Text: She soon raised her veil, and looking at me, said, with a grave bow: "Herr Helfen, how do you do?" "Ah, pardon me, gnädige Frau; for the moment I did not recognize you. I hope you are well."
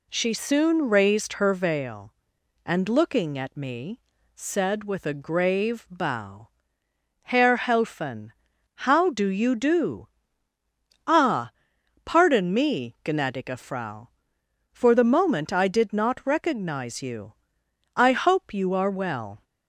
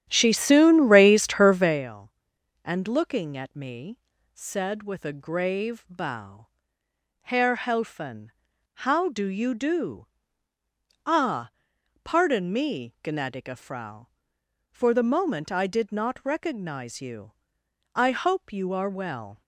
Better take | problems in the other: first | starts louder than the rest; strong; until 1.9 s; 10.5 dB

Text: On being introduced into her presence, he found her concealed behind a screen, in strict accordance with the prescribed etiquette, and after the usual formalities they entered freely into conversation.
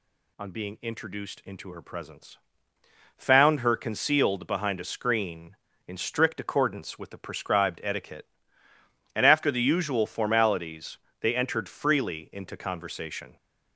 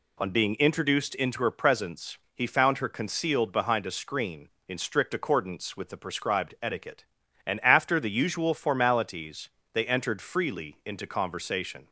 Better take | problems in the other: second | skips "he"; at 2.7 s // pauses between "formalities" and "they"; slight; at 10.9 s; 0.22 s long; slight in the second

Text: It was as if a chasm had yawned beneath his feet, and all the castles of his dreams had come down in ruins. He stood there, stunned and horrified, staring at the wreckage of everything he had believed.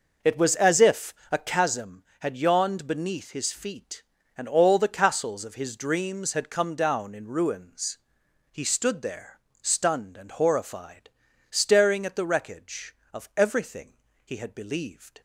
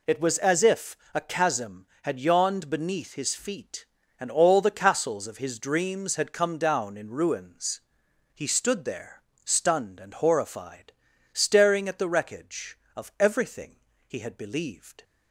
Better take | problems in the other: second | starts louder than the rest; noticeable; until 1.7 s; 5.5 dB // pauses between "if" and "a"; slight; at 1.1 s; 0.16 s long; slight in the second // pauses between "everything" and "he"; slight; at 13.9 s; 0.30 s long; slight in the second

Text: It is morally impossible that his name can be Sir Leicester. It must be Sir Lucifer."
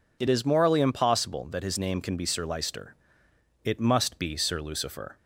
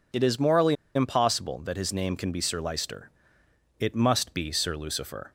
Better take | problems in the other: first | pauses between "morally" and "impossible"; slight; at 0.7 s; 0.21 s long

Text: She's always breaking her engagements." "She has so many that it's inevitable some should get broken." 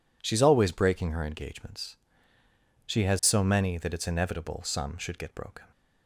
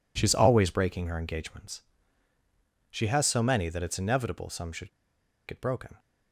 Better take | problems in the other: first | pauses between "should" and "get"; noticeable; at 4.8 s; 0.58 s long

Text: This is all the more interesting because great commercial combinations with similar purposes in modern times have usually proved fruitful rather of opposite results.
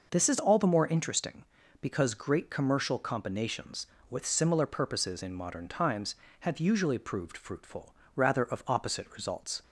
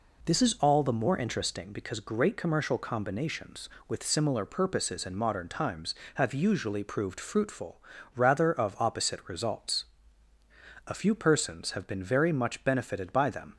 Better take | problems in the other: first | pauses between "fruitful" and "rather"; slight; at 7.7 s; 0.36 s long; slight in the first // goes on to say "A few persons have been very much benefited by them"; strong; from 10.8 s on; 2.6 s long

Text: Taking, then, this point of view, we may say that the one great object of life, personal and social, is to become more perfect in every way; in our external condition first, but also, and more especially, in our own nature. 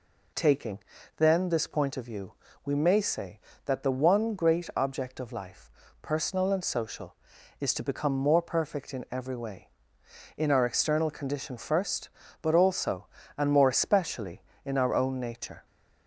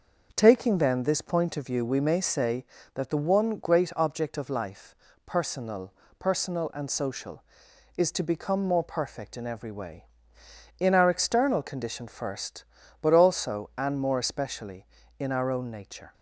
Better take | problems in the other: first | starts louder than the rest; noticeable; until 1.3 s; 6 dB // says "personal" twice; at 6.1 s

